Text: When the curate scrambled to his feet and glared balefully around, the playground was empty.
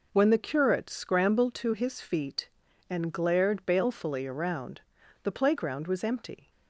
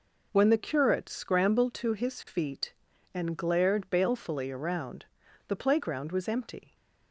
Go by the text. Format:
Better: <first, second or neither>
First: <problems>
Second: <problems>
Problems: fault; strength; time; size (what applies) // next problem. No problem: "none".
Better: neither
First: none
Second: none